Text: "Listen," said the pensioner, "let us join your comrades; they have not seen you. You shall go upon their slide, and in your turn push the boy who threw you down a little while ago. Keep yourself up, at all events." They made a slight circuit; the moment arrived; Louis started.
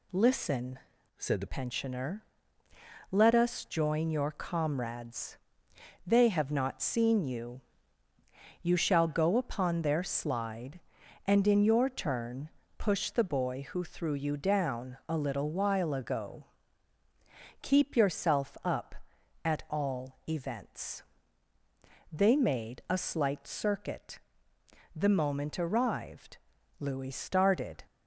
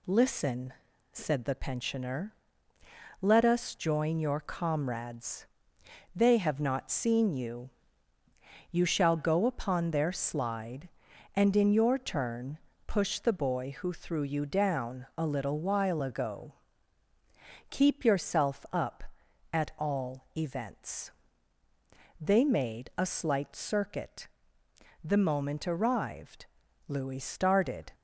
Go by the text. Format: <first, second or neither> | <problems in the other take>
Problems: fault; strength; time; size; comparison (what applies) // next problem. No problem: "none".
second | changes voice from "said" to "the"; from 1.1 to 1.4 s; 0.3 s long // pauses between "turn" and "push"; slight; at 12.4 s; 0.30 s long; slight in the second